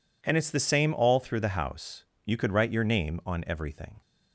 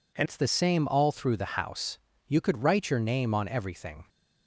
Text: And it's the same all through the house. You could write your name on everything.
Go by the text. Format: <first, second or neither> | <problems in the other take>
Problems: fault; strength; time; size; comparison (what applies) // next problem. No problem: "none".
first | changes voice at "it's"; from 0.2 s on; 3.8 s long